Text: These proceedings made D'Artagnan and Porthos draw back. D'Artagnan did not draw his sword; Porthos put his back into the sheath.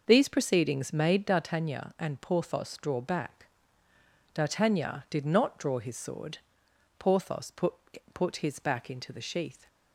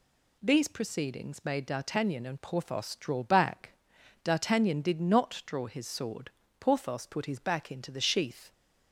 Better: second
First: says "put" twice; at 8.1 s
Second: none

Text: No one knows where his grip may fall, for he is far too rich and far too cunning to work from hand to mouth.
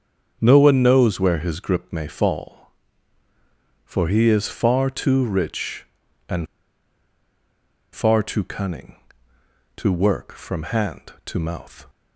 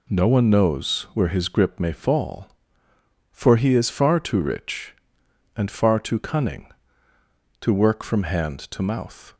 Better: second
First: starts louder than the rest; until 1.4 s; 7 dB // pauses between "and" and "far"; strong; at 6.4 s; 1.4 s long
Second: none

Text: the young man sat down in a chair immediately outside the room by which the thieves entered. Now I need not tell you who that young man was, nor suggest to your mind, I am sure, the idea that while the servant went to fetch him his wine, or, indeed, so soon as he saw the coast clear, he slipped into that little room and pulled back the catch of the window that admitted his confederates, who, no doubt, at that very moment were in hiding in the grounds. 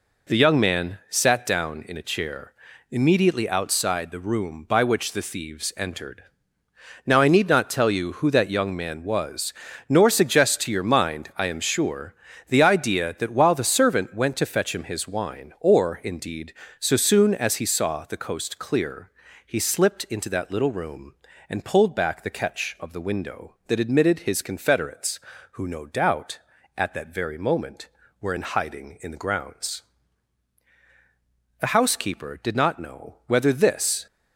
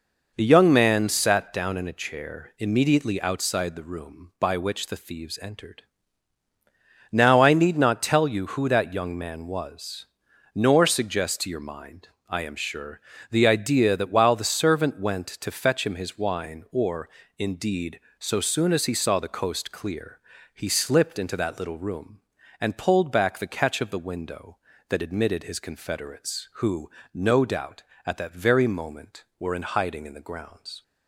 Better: second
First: pauses between "chair" and "immediately"; at 2.5 s; 0.38 s long // goes on to say "The housekeeper did not know whether this"; strong; from 31.6 s on; 2.4 s long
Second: none

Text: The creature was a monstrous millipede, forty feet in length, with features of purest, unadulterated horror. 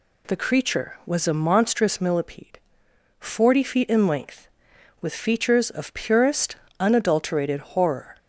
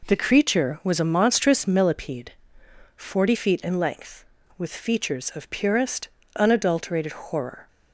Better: neither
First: none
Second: none

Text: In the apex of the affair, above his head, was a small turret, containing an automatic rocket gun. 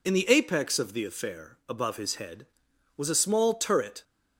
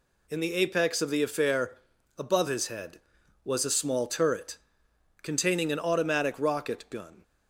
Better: second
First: stops before "containing an automatic rocket gun"; at 4.0 s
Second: none

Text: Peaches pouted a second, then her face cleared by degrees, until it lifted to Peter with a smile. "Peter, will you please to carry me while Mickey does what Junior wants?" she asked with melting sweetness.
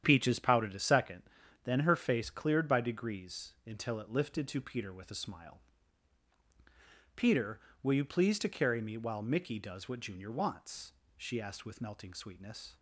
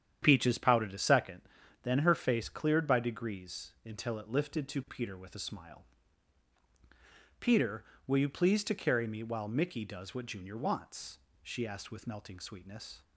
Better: neither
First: starts louder than the rest; strong; until 1.0 s; 9.5 dB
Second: starts louder than the rest; strong; until 1.2 s; 9.5 dB

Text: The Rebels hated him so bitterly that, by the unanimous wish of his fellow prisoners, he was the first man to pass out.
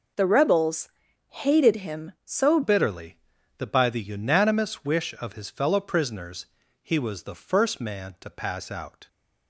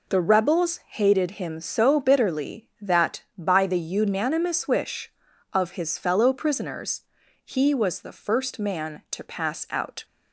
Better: second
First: pauses between "Rebels" and "hated"; at 0.8 s; 0.40 s long // changes voice at "bitterly"; from 2.6 s on; 6.4 s long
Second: none

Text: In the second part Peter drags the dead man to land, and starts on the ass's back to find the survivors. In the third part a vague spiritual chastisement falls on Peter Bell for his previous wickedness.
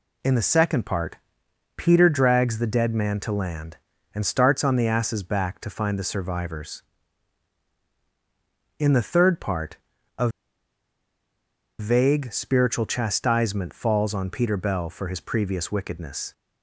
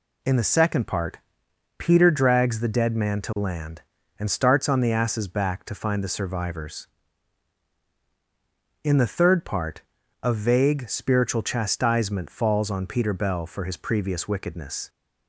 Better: second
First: pauses between "part" and "Peter"; noticeable; at 1.1 s; 0.60 s long // pauses between "part" and "a"; at 9.7 s; 0.40 s long // pauses between "a" and "vague"; strong; at 10.2 s; 1.5 s long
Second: pauses between "part" and "Peter"; noticeable; at 1.1 s; 0.60 s long // pauses between "part" and "a"; at 9.8 s; 0.40 s long

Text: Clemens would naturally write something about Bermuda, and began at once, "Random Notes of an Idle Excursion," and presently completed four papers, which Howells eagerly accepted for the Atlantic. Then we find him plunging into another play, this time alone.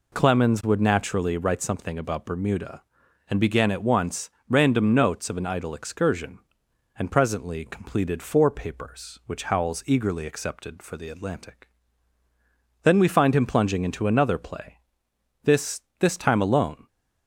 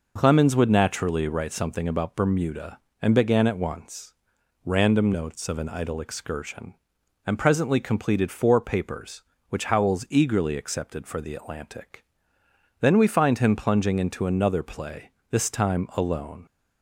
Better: second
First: says "this" twice; at 16.0 s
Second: none

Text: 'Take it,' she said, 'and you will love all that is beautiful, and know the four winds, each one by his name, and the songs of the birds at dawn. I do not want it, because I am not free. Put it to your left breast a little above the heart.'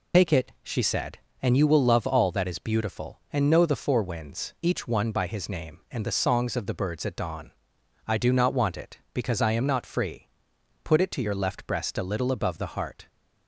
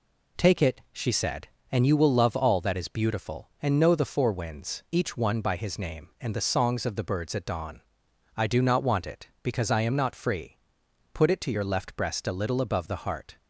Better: second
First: loses the start of "Take"; at 0.1 s; 85 ms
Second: none

